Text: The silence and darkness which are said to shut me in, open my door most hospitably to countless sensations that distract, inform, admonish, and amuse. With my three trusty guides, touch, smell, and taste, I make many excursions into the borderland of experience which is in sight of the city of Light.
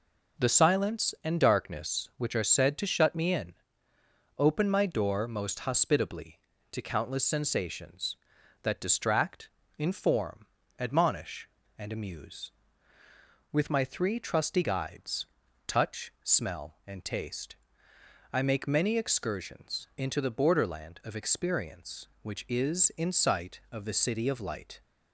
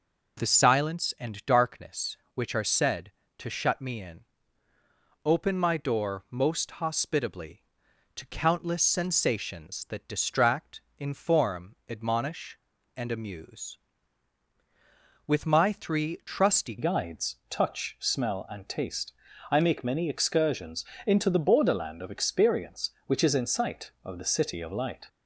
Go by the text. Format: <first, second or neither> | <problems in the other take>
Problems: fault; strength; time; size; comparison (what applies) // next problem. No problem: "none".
first | changes voice at "guides"; from 16.7 s on; 8.3 s long // pauses between "excursions" and "into"; slight; at 20.8 s; 0.22 s long